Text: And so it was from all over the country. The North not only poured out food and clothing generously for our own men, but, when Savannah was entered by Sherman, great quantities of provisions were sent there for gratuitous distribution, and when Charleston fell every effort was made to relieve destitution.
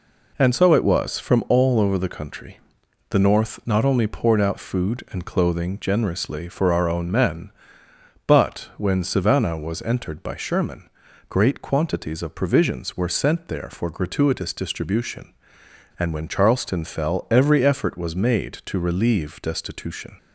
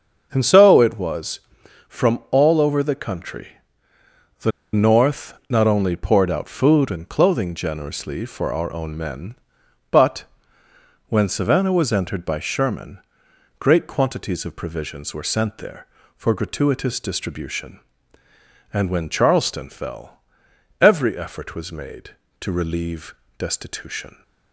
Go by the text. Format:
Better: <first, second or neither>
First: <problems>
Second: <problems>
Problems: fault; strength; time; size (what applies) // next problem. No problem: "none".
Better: first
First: none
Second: starts louder than the rest; until 1.3 s; 7 dB // pauses between "The" and "North"; slight; at 4.5 s; 0.23 s long // pauses between "fell" and "every"; noticeable; at 20.2 s; 0.60 s long // pauses between "relieve" and "destitution"; slight; at 23.1 s; 0.24 s long